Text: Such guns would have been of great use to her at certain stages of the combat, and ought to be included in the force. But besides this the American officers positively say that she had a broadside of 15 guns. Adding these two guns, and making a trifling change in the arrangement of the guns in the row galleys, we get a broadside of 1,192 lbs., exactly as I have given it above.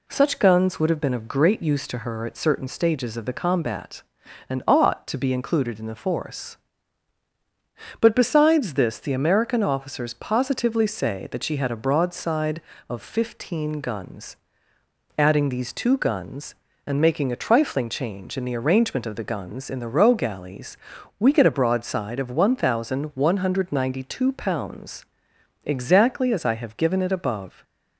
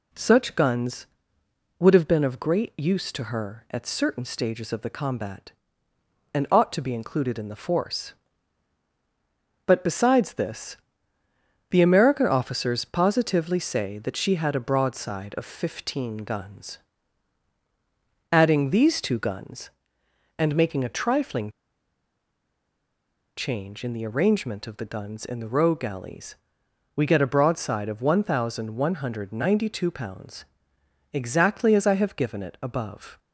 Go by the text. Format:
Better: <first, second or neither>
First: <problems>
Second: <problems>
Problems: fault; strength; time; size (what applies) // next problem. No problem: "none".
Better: first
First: none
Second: pauses between "this" and "the"; noticeable; at 10.7 s; 0.94 s long // pauses between "trifling" and "change"; strong; at 21.4 s; 1.8 s long